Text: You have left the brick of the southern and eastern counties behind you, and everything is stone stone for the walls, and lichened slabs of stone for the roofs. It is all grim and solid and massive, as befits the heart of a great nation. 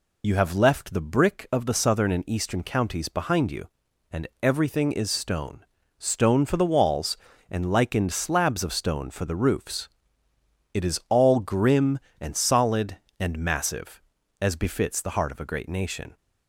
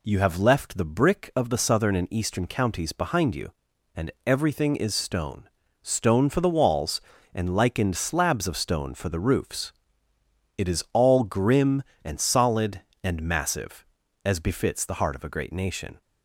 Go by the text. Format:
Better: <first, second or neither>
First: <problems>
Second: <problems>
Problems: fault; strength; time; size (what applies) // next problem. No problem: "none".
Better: second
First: loses the start of "You"; at 0.2 s; 60 ms // pauses between "stone" and "stone"; slight; at 5.6 s; 0.36 s long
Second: pauses between "stone" and "stone"; slight; at 5.4 s; 0.36 s long